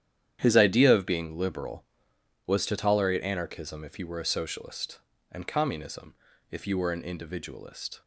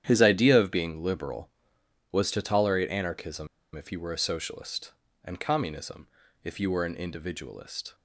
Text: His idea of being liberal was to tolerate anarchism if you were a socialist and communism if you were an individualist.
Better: first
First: starts louder than the rest; strong; until 1.4 s; 10 dB // pauses between "communism" and "if"; at 6.1 s; 0.38 s long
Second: starts louder than the rest; strong; until 1.0 s; 10 dB // pauses between "anarchism" and "if"; slight; at 3.4 s; 0.27 s long // pauses between "communism" and "if"; at 6.0 s; 0.38 s long

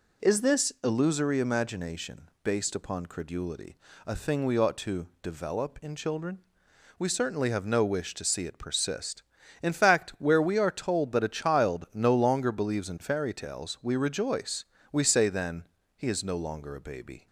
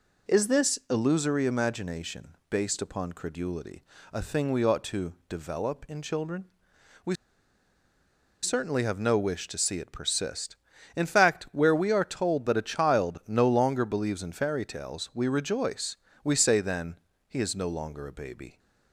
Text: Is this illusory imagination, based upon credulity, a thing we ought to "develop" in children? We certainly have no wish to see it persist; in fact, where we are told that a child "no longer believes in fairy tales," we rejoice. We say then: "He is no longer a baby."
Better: first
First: pauses between "to" and "develop"; slight; at 5.0 s; 0.16 s long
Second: pauses between "to" and "develop"; slight; at 5.1 s; 0.16 s long // pauses between "We" and "certainly"; strong; at 7.1 s; 1.2 s long

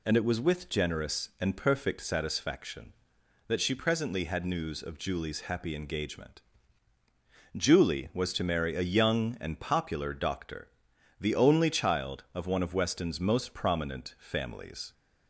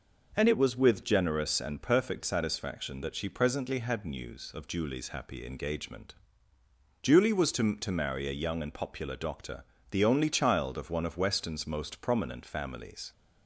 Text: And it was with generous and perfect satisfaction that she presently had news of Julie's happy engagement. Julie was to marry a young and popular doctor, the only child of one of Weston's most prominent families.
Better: first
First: none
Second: says "to" twice; at 7.7 s

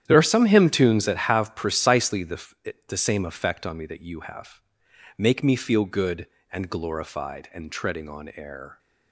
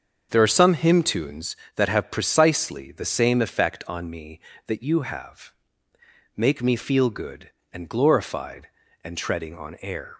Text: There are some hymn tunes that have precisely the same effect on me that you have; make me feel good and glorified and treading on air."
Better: second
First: starts louder than the rest; strong; until 1.0 s; 10.5 dB // says "the" twice; at 2.8 s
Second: starts louder than the rest; until 1.3 s; 7 dB

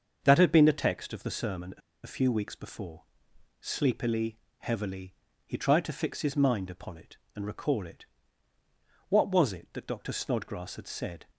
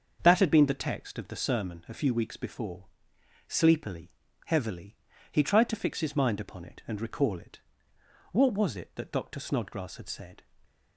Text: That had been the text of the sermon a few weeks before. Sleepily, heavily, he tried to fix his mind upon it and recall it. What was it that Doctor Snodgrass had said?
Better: second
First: starts louder than the rest; until 1.2 s; 6.5 dB // pauses between "a" and "few"; slight; at 1.8 s; 0.25 s long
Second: starts louder than the rest; until 1.2 s; 6.5 dB

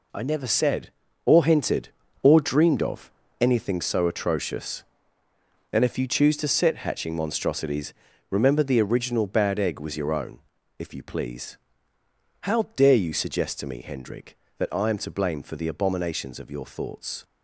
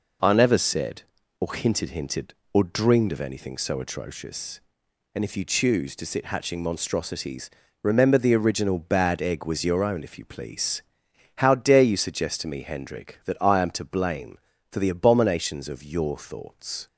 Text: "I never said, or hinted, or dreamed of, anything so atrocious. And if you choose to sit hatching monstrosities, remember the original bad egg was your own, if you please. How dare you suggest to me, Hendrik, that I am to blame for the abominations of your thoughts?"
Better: first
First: none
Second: says "hinted" twice; at 1.9 s

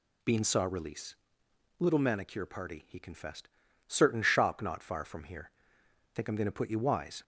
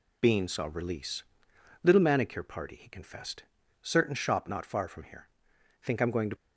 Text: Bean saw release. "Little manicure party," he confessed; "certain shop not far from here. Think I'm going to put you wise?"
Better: first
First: none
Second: stops before "put you wise"; at 6.3 s

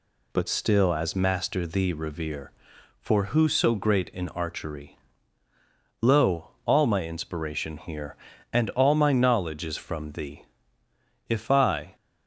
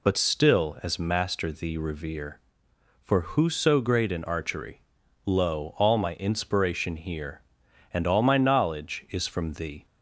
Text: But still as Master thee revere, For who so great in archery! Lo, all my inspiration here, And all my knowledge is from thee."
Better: second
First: goes on to say "If I"; noticeable; from 11.2 s on; 0.66 s long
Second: none

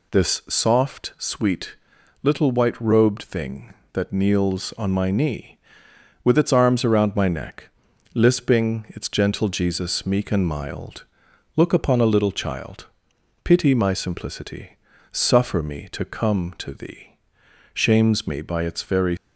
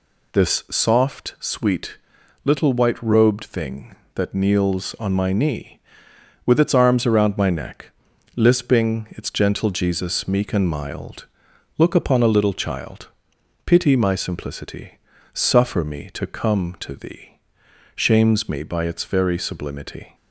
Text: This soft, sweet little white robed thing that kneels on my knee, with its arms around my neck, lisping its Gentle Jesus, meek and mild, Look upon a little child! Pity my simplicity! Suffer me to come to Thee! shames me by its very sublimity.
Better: second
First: pauses between "sweet" and "little"; noticeable; at 1.7 s; 0.48 s long // stops before "sublimity"; at 19.1 s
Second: pauses between "sweet" and "little"; noticeable; at 1.9 s; 0.48 s long

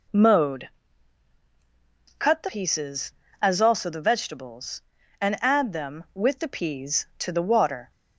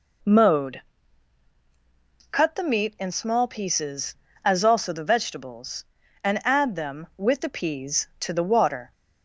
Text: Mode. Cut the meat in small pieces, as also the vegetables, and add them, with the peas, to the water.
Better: second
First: skips "meat in small"; at 2.4 s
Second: none

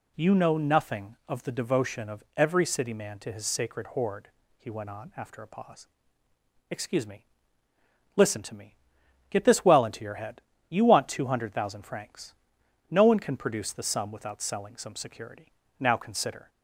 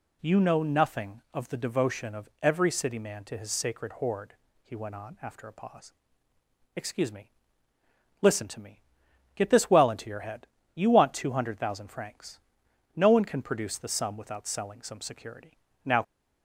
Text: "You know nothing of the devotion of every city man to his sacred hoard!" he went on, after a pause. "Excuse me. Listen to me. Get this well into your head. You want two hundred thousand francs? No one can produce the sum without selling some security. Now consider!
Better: first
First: none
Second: stops before "consider"; at 16.0 s

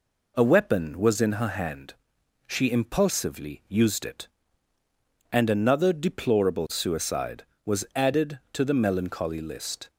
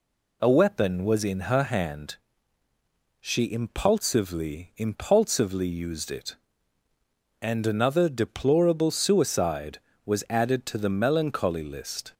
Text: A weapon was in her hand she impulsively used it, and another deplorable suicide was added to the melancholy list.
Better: first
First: pauses between "hand" and "she"; noticeable; at 1.9 s; 0.54 s long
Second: pauses between "hand" and "she"; at 2.1 s; 1.0 s long // says "impulsively" twice; at 4.7 s

